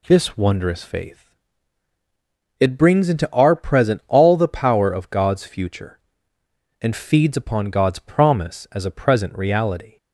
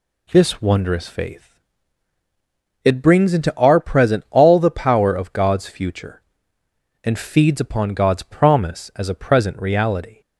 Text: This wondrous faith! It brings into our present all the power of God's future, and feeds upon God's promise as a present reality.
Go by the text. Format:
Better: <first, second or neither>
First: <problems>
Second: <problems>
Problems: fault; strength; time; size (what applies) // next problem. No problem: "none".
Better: neither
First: none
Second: none